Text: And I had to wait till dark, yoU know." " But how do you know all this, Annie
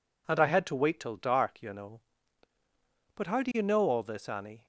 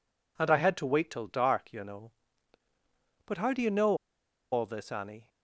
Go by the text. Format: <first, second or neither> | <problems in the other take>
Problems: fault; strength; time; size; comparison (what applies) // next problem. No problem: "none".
first | pauses between "know" and "all"; noticeable; at 3.9 s; 0.55 s long